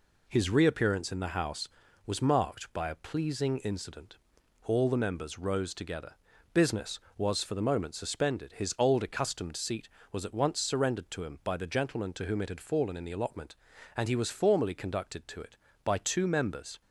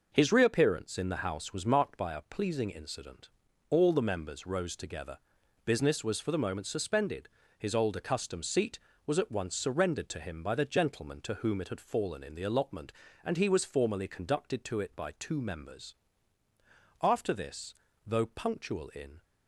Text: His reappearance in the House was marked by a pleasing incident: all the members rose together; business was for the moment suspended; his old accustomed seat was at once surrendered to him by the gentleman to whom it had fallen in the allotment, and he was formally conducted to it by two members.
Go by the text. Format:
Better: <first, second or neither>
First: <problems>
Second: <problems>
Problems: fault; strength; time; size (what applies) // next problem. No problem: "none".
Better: first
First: none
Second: goes on to say "After this though punctual in"; strong; from 17.0 s on; 2.2 s long